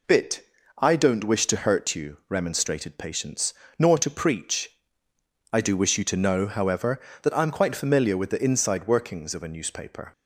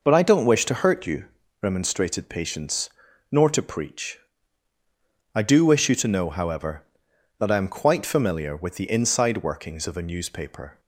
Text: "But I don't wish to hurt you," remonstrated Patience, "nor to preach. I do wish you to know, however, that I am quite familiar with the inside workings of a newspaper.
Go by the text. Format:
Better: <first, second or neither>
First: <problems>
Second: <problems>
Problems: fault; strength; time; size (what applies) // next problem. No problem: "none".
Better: second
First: says "Bit" for "But"; at 0.0 s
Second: none